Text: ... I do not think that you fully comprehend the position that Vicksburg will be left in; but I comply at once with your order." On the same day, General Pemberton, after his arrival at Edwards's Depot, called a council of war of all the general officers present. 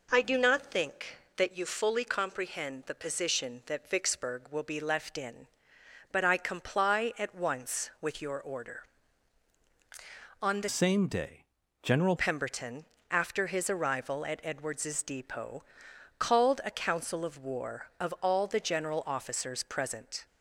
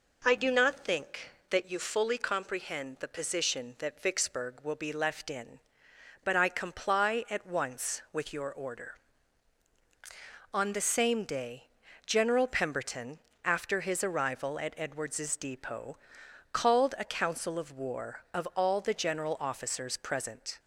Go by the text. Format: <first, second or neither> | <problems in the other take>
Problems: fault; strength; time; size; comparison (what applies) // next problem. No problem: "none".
second | changes voice from "same" to "General"; from 10.6 to 12.1 s; 1.5 s long